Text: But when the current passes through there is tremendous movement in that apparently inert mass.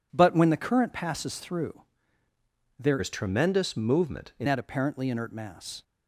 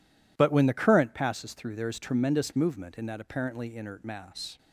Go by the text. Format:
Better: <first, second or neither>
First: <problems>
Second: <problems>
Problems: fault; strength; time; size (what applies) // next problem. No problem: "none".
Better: second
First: pauses between "through" and "there"; at 1.8 s; 1.0 s long // changes voice from "is" to "in"; from 2.9 to 4.4 s; 1.5 s long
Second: none